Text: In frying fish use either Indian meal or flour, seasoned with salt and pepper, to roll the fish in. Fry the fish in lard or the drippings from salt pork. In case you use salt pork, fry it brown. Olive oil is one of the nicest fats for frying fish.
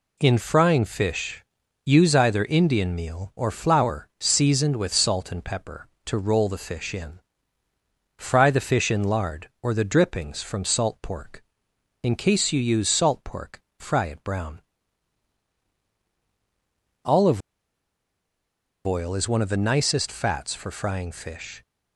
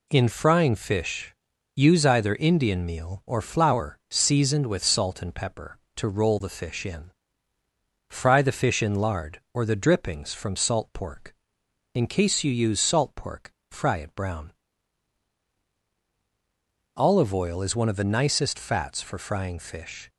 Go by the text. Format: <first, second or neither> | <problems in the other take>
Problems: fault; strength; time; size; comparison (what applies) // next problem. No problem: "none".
second | pauses between "fish" and "use"; at 1.4 s; 0.42 s long; also in the second // pauses between "Olive" and "oil"; strong; at 17.3 s; 1.4 s long